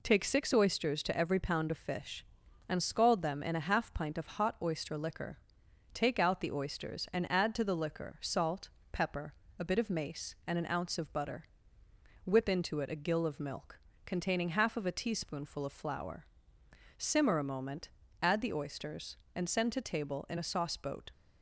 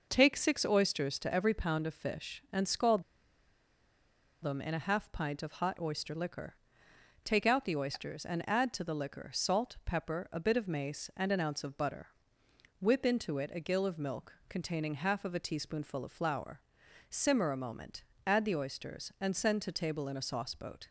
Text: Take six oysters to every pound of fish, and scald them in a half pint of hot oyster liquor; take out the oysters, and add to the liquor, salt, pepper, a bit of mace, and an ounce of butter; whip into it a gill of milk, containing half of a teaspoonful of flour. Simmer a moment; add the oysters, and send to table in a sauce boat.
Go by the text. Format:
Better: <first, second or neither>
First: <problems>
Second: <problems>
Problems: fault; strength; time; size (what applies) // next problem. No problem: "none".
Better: first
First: none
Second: pauses between "scald" and "them"; strong; at 3.0 s; 1.3 s long